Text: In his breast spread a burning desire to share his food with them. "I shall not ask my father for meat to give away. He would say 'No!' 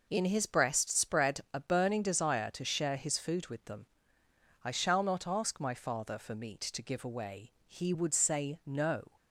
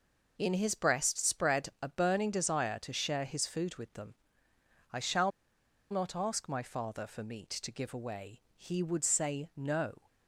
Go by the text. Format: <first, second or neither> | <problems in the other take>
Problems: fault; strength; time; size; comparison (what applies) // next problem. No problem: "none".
first | pauses between "shall" and "not"; noticeable; at 5.2 s; 0.60 s long